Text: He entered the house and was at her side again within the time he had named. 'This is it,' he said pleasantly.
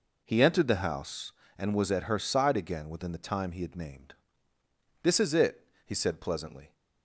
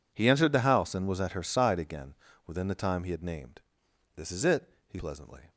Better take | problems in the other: first | pauses between "again" and "within"; slight; at 2.1 s; 0.32 s long // skips "said"; at 4.9 s

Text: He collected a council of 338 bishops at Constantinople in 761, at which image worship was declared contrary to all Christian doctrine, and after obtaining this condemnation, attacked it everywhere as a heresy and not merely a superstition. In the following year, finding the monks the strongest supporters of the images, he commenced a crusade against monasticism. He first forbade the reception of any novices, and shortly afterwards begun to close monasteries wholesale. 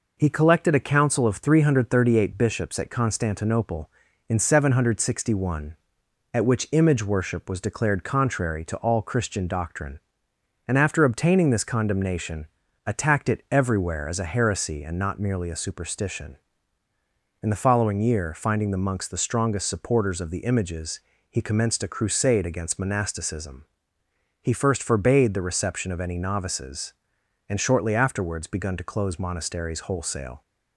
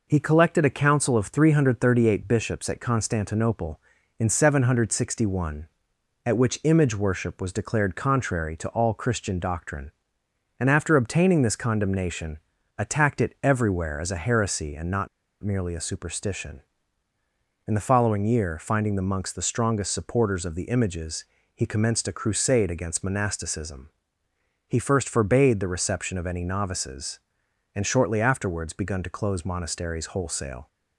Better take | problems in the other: first | pauses between "not" and "merely"; slight; at 15.0 s; 0.35 s long

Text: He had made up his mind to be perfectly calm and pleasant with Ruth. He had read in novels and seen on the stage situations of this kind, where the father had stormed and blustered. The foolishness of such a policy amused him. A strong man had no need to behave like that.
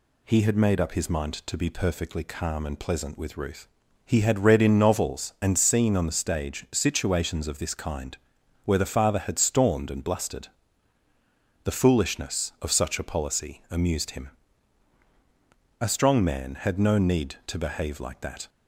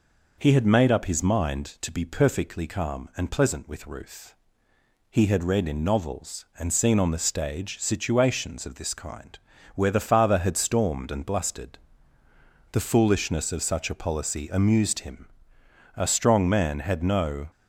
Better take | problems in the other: first | stops before "need to behave like that"; at 17.5 s

